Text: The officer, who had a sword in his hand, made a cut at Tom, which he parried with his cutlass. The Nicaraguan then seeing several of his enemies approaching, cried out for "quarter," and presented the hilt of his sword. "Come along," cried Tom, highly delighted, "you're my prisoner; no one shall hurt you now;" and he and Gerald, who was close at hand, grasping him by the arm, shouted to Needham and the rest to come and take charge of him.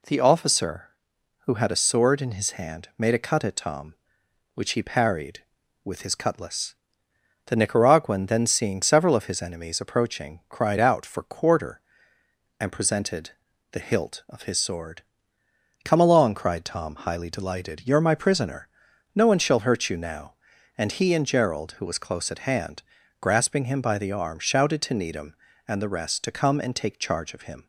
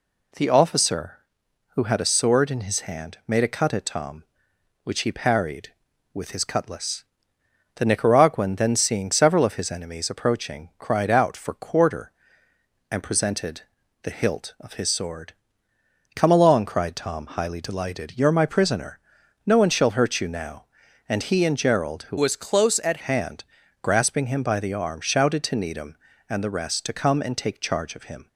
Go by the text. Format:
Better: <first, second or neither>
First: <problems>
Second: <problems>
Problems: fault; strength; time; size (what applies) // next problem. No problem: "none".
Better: first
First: pauses between "presented" and "the"; at 13.3 s; 0.40 s long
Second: pauses between "presented" and "the"; at 13.6 s; 0.40 s long // changes voice from "was" to "at"; from 22.1 to 22.9 s; 0.8 s long